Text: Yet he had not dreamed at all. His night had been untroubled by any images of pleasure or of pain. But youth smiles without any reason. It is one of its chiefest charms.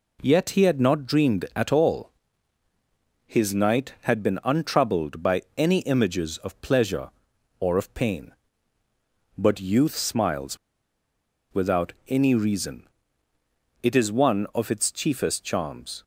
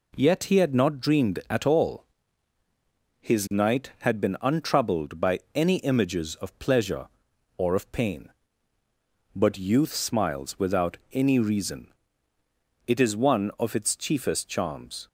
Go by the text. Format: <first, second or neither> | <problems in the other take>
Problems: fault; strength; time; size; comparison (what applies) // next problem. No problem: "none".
second | pauses between "smiles" and "without"; noticeable; at 10.5 s; 0.95 s long